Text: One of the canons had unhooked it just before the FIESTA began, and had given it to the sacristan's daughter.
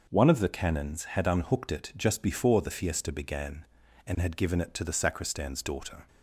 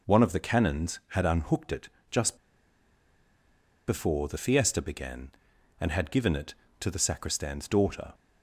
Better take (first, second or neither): first